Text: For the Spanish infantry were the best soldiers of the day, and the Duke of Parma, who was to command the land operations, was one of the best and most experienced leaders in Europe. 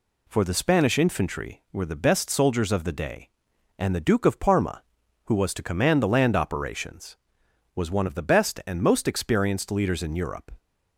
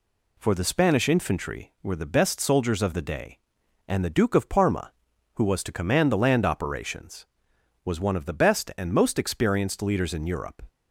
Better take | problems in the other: neither | none

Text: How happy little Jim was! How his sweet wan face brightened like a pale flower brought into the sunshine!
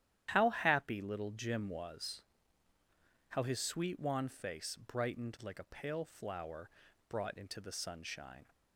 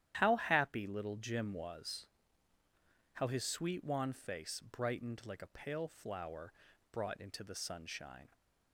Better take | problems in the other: neither | starts louder than the rest; strong; the same in both // pauses between "flower" and "brought"; the same in both

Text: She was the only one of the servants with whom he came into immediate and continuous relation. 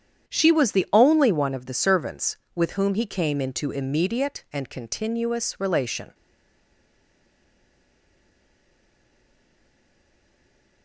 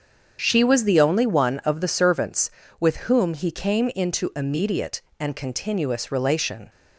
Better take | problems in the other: second | starts louder than the rest; strong; until 1.3 s; 9 dB; strong in the second // stays silent after the last word; strong; from 6.1 s on; 4.7 s long

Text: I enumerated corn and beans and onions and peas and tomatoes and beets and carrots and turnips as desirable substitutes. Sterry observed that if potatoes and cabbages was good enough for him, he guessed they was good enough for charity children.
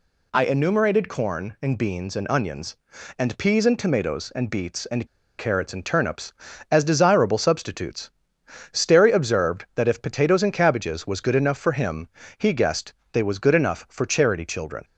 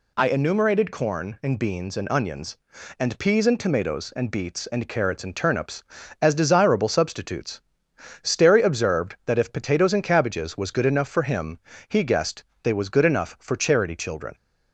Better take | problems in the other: second | pauses between "and" and "carrots"; slight; at 5.0 s; 0.30 s long // pauses between "guessed" and "they"; slight; at 12.9 s; 0.20 s long; slight in the second

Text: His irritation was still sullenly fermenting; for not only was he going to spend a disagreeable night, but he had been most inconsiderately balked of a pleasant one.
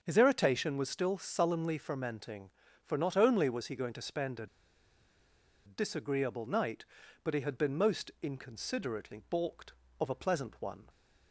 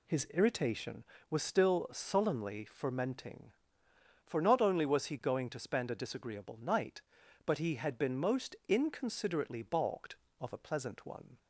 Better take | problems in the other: second | starts louder than the rest; until 1.0 s; 6.5 dB // pauses between "a" and "disagreeable"; at 4.4 s; 1.1 s long

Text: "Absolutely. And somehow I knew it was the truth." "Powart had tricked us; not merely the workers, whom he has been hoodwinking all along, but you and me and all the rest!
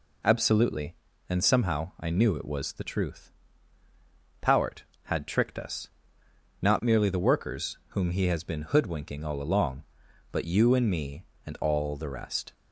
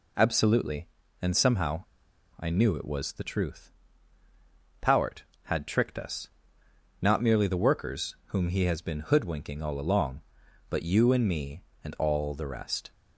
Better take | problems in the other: first | pauses between "somehow" and "I"; noticeable; at 1.8 s; 0.55 s long

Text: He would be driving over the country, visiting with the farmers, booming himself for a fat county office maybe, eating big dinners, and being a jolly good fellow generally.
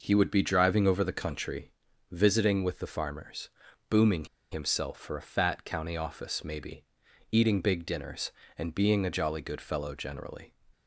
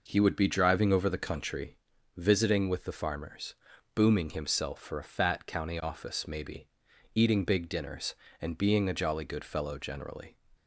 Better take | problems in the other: second | pauses between "booming" and "himself"; slight; at 4.2 s; 0.26 s long

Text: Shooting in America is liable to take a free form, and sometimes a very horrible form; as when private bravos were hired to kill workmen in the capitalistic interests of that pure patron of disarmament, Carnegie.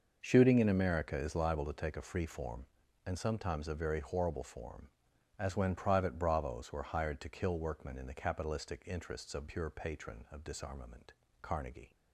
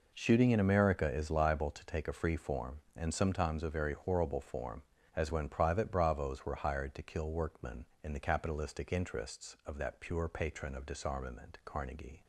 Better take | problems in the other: second | skips "that"; at 9.4 s

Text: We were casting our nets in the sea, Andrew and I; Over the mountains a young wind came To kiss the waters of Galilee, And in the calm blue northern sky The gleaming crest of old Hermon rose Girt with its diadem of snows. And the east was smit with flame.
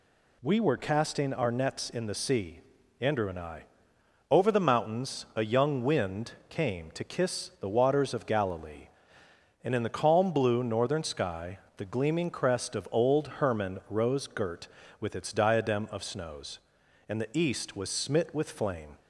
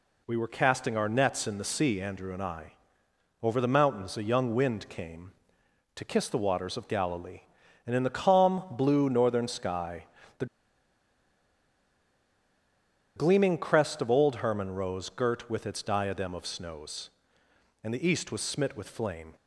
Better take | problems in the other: first | pauses between "sky" and "The"; slight; at 10.0 s; 0.32 s long; slight in the first // pauses between "The" and "gleaming"; strong; at 10.4 s; 2.6 s long

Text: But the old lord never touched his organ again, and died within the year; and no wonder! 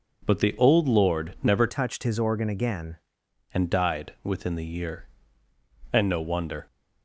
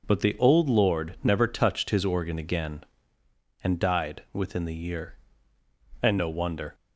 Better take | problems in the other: second | changes voice from "touched" to "again"; from 1.6 to 2.9 s; 1.3 s long

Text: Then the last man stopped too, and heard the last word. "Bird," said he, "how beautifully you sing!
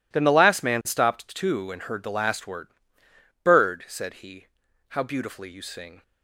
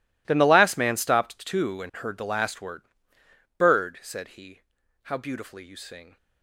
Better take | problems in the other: first | gets quieter; strong; throughout; 19 dB

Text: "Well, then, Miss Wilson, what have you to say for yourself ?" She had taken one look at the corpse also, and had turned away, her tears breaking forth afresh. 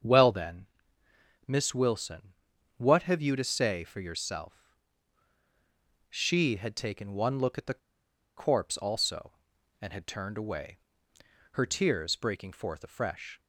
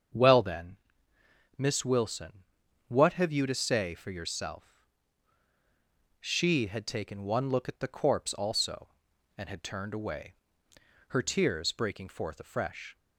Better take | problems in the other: second | starts louder than the rest; strong; until 1.8 s; 8.5 dB; strong in the second // pauses between "the" and "corpse"; noticeable; at 7.7 s; 0.57 s long

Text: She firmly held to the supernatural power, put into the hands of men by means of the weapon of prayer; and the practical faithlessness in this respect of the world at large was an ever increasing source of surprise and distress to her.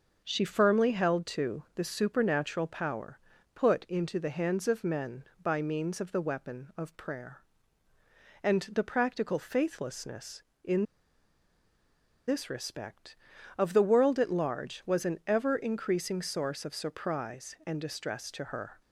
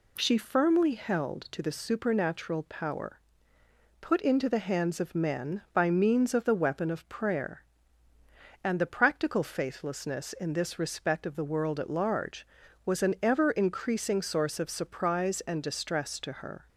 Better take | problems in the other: second | starts louder than the rest; until 1.2 s; 6.5 dB // pauses between "in" and "this"; strong; at 10.8 s; 1.4 s long

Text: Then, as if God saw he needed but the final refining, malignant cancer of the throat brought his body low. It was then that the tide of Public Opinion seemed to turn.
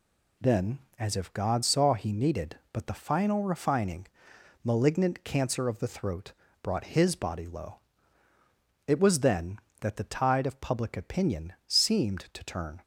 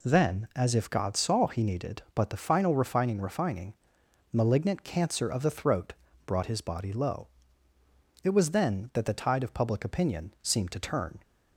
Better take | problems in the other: first | says "refining" twice; at 3.2 s // pauses between "throat" and "brought"; slight; at 5.9 s; 0.32 s long; slight in the first

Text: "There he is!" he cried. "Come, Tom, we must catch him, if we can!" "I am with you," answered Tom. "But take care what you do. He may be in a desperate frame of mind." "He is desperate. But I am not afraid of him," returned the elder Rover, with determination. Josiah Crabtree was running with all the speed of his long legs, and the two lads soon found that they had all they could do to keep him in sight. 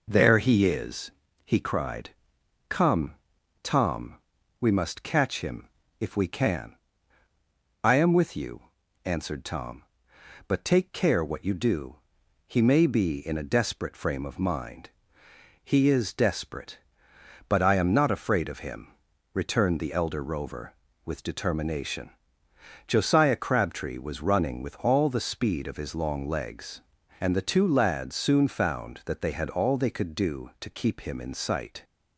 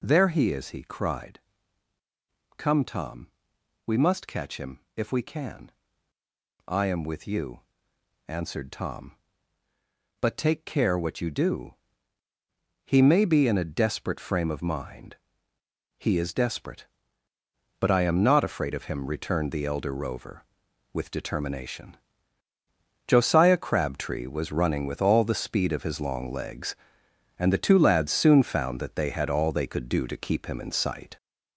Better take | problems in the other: first | gets louder; noticeable; throughout; 5 dB

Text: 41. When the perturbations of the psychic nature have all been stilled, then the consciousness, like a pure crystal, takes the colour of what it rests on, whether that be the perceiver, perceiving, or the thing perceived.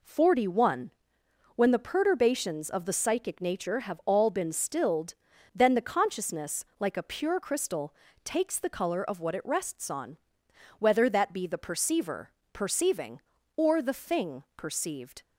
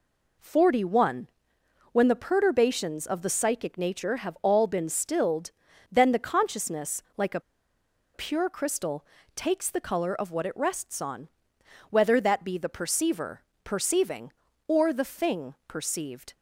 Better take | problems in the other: first | pauses between "a" and "pure"; noticeable; at 7.3 s; 0.74 s long

